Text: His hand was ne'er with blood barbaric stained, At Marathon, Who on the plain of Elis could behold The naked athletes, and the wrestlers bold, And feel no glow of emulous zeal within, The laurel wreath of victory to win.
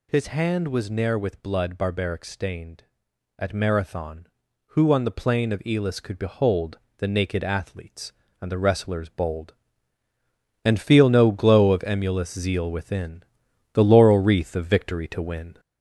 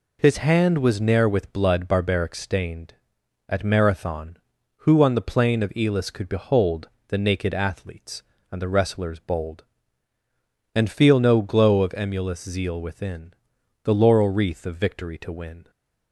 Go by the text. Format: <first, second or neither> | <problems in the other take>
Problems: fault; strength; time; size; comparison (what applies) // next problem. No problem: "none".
second | gets louder; throughout; 3.5 dB // pauses between "behold" and "The"; slight; at 6.7 s; 0.18 s long; slight in the second